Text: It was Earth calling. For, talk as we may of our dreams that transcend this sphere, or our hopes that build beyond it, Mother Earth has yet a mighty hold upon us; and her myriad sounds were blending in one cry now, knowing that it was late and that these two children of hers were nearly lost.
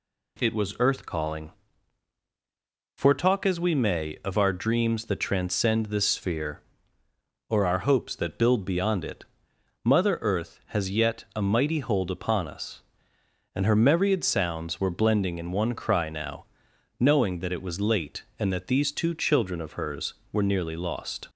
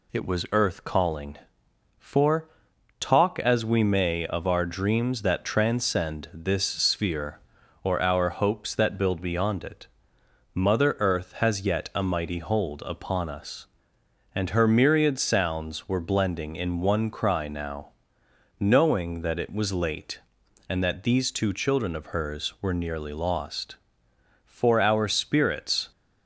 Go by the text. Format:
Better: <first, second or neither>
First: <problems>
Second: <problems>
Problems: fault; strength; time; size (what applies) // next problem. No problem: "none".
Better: first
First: none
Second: goes on to say "For our spirits"; from 24.4 s on; 1.4 s long